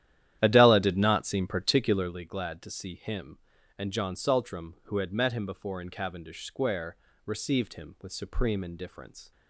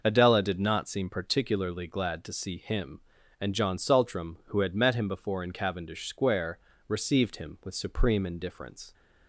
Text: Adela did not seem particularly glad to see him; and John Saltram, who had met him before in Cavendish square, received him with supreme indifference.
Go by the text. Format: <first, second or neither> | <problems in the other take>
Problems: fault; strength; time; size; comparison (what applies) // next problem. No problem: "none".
second | starts louder than the rest; strong; until 2.2 s; 11.5 dB